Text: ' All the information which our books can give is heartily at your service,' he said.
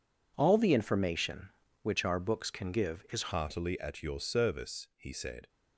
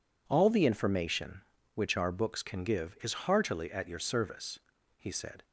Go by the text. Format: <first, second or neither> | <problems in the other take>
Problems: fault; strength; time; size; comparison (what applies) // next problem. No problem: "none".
second | changes voice at "heartily"; from 3.3 s on; 2.1 s long